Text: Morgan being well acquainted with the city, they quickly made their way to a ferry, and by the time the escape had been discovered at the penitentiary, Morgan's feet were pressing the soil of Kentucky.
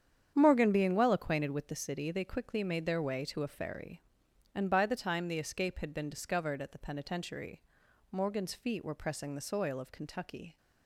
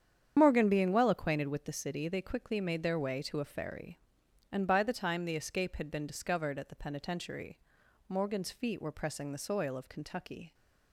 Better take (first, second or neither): first